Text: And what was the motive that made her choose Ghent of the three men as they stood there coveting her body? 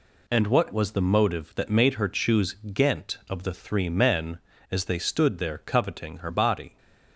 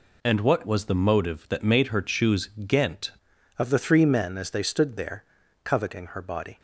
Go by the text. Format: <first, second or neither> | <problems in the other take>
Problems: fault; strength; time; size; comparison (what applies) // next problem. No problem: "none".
first | pauses between "choose" and "Ghent"; slight; at 2.5 s; 0.16 s long; slight in the first // changes voice at "of"; from 3.5 s on; 3.0 s long // pauses between "there" and "coveting"; at 5.2 s; 0.40 s long